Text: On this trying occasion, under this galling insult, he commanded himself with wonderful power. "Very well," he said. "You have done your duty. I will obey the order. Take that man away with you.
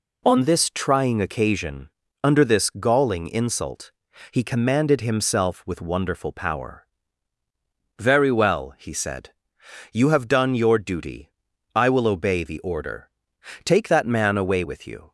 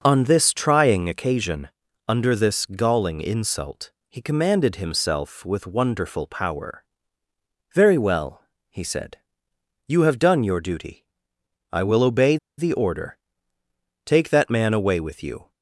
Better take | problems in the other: first | pauses between "obey" and "the"; slight; at 12.3 s; 0.21 s long

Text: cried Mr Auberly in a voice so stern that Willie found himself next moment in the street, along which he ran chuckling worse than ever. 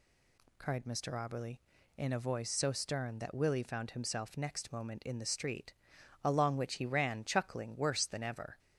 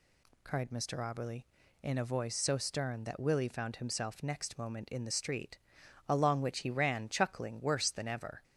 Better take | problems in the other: neither | none

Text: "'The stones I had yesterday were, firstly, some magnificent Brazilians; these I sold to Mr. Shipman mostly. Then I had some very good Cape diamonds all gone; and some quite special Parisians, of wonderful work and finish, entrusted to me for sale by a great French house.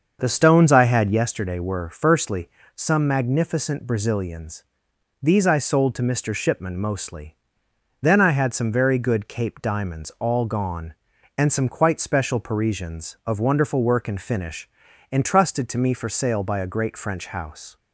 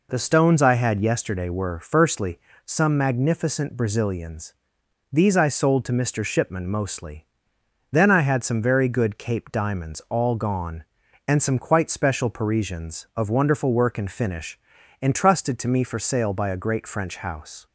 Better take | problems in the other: second | starts louder than the rest; until 1.3 s; 6.5 dB

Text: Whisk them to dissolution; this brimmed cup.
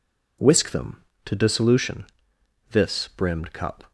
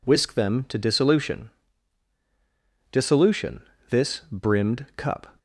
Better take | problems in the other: first | says "dissolution" twice; at 2.9 s

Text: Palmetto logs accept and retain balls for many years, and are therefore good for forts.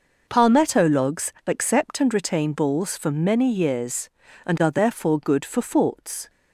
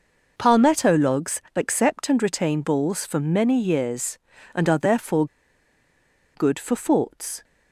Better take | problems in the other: first | pauses between "therefore" and "good"; at 5.2 s; 1.0 s long

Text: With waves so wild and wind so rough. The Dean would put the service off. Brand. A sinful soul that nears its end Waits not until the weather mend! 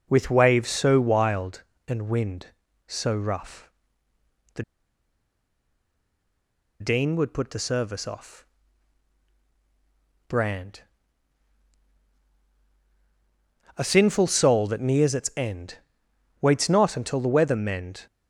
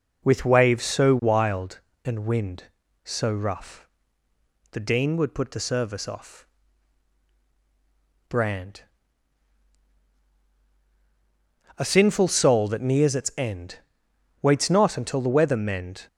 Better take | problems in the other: second | pauses between "The" and "Dean"; strong; at 4.6 s; 2.1 s long // pauses between "end" and "Waits"; noticeable; at 15.7 s; 0.62 s long; noticeable in the second

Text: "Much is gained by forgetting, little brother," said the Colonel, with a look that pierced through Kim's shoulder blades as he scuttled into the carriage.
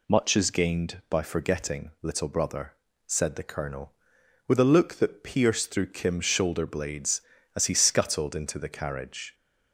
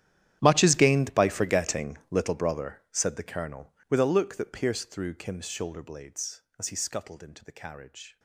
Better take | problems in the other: first | gets quieter; strong; throughout; 20.5 dB

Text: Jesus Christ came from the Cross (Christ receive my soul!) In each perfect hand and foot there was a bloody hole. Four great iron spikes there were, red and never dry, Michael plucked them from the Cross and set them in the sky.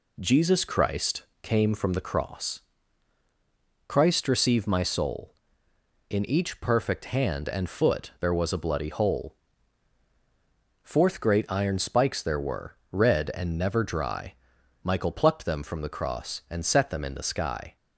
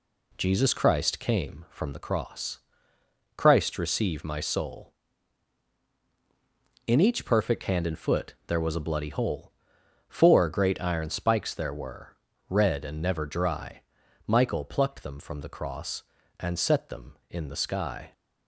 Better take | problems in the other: second | pauses between "Christ" and "came"; slight; at 1.2 s; 0.18 s long // says "Fourth" for "Four"; at 10.8 s

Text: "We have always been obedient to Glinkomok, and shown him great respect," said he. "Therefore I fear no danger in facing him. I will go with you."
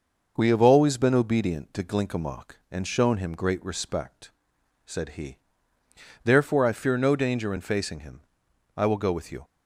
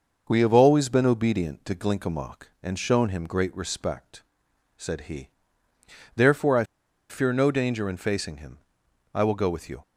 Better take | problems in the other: first | pauses between "I" and "fear"; at 6.6 s; 0.45 s long

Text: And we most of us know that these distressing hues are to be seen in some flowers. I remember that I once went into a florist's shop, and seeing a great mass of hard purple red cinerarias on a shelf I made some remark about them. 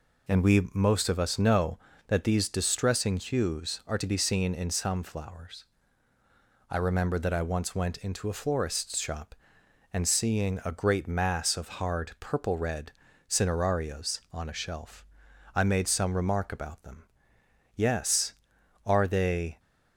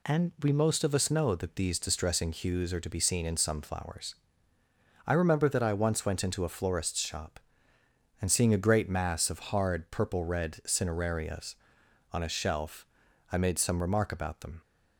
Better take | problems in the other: second | pauses between "red" and "cinerarias"; at 12.9 s; 0.38 s long // pauses between "shelf" and "I"; noticeable; at 15.0 s; 0.48 s long; noticeable in the second // goes on to say "Yes are they"; strong; from 17.7 s on; 1.8 s long

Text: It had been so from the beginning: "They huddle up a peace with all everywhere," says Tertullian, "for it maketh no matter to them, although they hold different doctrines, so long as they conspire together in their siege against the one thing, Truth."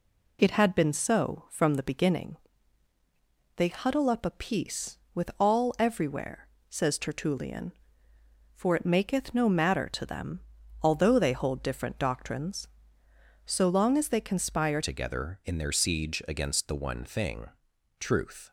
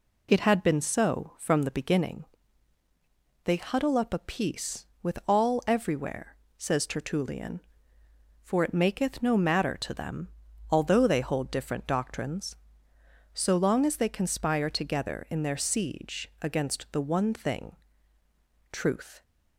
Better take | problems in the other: second | changes voice at "together"; from 14.8 s on; 3.7 s long

